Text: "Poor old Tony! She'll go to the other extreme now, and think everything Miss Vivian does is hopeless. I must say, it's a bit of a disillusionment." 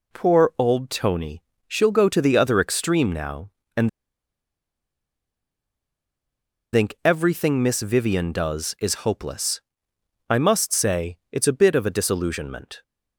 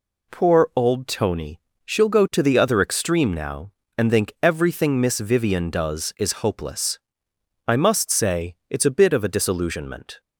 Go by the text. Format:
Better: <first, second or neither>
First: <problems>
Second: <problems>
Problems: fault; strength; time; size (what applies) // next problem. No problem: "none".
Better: second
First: pauses between "and" and "think"; strong; at 3.8 s; 2.8 s long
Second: none